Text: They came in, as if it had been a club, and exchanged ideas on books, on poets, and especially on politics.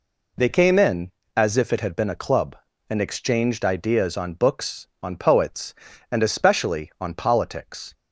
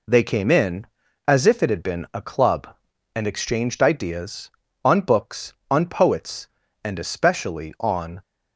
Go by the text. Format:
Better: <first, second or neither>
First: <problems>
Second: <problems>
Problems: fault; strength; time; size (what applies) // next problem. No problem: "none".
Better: first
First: none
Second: stops before "politics"; at 8.2 s